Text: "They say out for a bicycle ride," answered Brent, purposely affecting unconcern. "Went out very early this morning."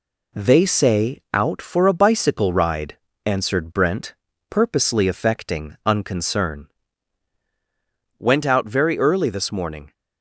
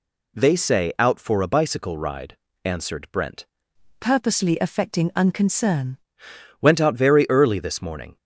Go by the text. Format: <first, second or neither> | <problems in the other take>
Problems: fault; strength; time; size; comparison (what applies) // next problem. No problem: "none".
first | changes voice from "purposely" to "unconcern"; from 3.9 to 5.9 s; 2.0 s long